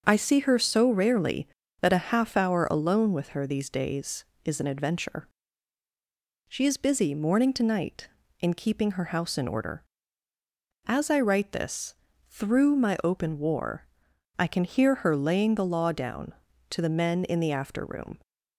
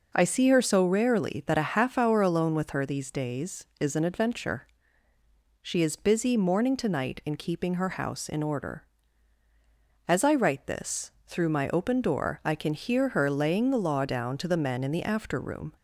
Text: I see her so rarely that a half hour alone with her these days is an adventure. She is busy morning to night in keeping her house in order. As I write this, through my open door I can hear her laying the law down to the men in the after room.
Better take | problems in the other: second | starts louder than the rest; until 1.0 s; 6.5 dB // says "war" for "door"; at 13.3 s

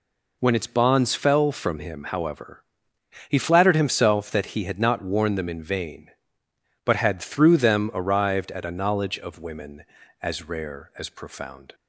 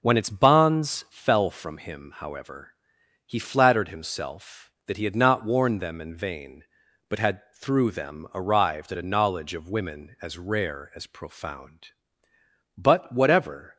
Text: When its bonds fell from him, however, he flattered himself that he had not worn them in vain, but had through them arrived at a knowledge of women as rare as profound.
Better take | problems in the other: first | goes on to say "But whatever"; noticeable; from 12.7 s on; 0.98 s long

